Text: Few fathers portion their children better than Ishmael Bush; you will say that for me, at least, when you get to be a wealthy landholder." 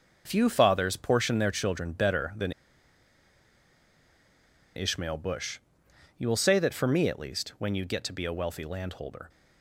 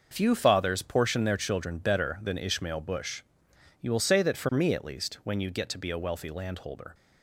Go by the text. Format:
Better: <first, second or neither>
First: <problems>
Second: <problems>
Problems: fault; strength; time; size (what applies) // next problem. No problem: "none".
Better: second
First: starts louder than the rest; noticeable; until 1.2 s; 6 dB // pauses between "than" and "Ishmael"; strong; at 2.5 s; 2.2 s long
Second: starts louder than the rest; noticeable; until 1.1 s; 6 dB